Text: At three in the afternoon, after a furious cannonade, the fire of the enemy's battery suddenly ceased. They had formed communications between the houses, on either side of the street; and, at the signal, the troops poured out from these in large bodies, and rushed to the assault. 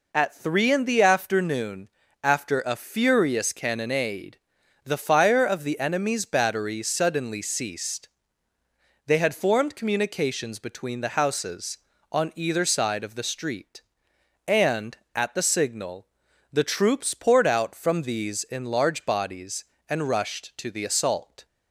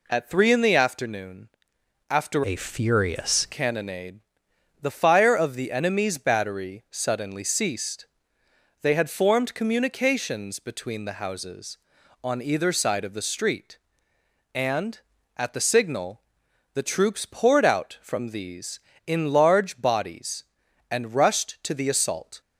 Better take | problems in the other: first | changes voice from "a" to "furious"; from 2.4 to 3.4 s; 1.0 s long

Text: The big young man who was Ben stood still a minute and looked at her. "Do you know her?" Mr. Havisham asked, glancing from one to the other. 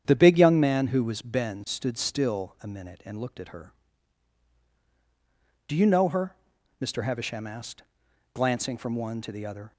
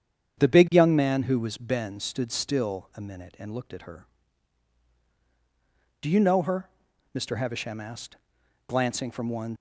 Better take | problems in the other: first | starts louder than the rest; strong; until 1.4 s; 8 dB; strong in the first // stops before "to the other"; at 9.5 s

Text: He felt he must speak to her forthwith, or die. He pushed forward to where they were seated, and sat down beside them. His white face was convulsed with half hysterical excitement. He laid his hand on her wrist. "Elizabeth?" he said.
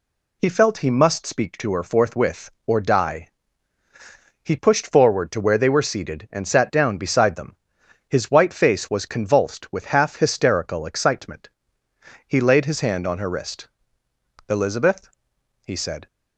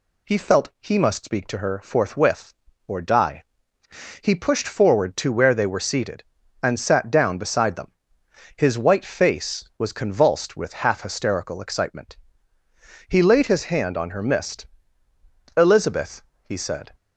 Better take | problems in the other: first | says "mist" for "wrist"; at 14.2 s

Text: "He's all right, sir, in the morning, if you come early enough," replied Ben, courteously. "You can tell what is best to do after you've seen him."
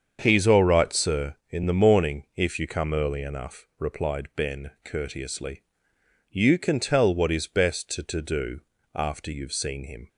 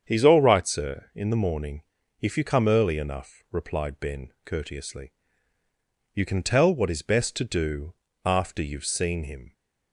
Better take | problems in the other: second | starts louder than the rest; strong; until 1.2 s; 7 dB; strong in the second // says "to" twice; at 8.0 s // pauses between "do" and "after"; slight; at 8.5 s; 0.34 s long; slight in the second

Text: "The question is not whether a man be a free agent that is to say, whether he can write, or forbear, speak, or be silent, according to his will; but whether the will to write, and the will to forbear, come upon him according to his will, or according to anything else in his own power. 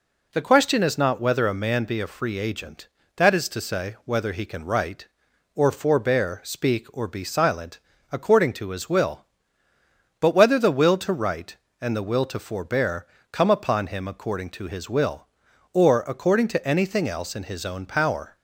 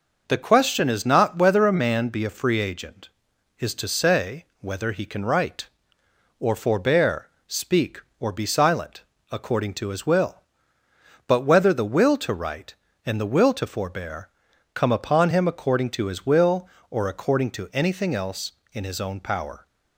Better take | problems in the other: first | skips "that"; at 3.3 s

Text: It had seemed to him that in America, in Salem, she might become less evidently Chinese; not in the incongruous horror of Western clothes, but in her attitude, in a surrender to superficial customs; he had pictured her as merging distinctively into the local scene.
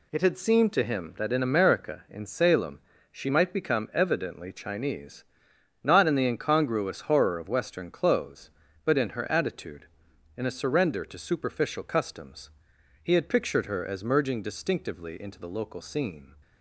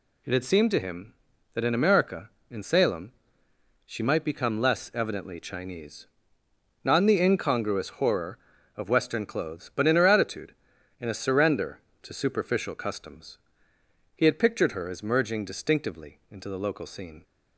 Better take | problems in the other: second | skips "less"; at 3.9 s

